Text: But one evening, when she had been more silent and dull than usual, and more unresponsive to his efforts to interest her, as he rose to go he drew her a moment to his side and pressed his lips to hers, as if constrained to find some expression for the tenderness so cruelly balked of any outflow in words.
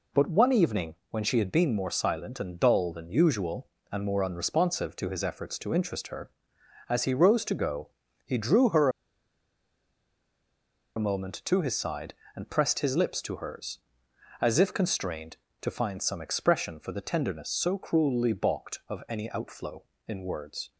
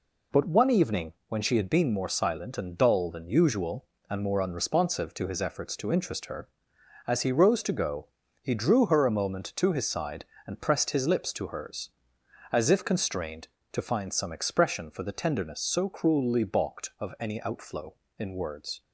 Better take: second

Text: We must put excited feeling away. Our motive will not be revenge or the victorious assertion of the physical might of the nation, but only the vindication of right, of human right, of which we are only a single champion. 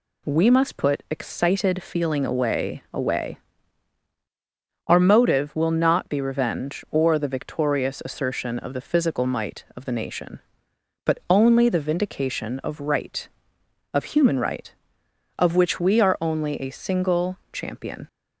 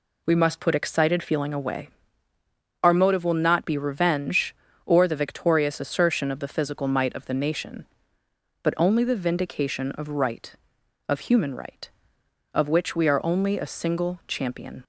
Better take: second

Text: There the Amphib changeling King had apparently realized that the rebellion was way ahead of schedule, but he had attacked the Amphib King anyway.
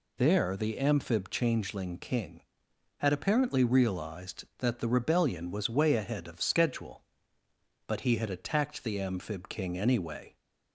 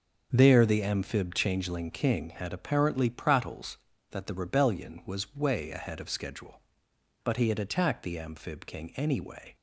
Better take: first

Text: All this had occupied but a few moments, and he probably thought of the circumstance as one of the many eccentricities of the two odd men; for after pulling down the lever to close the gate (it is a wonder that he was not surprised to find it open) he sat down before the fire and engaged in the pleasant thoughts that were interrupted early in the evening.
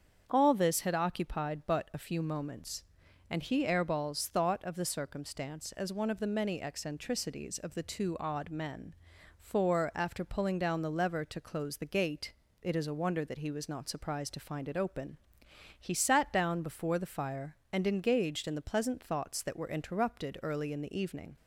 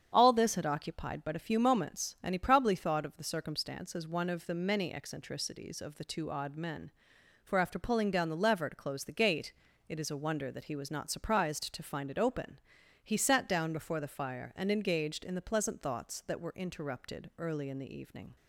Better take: second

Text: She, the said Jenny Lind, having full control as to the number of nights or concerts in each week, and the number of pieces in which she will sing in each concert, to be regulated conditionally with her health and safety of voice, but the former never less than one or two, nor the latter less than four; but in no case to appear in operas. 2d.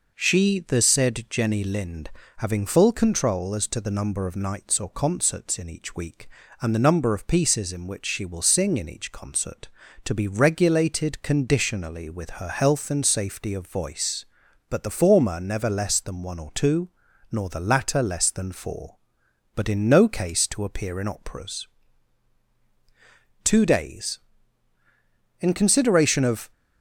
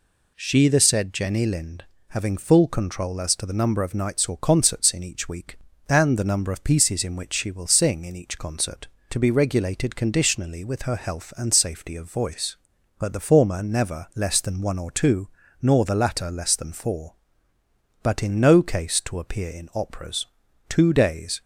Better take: second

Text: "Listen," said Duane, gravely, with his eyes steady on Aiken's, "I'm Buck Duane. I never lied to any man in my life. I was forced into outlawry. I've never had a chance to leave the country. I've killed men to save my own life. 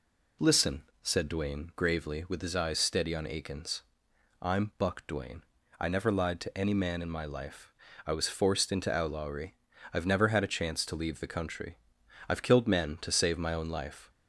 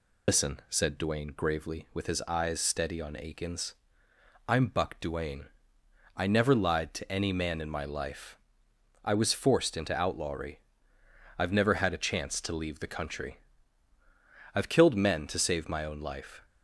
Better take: first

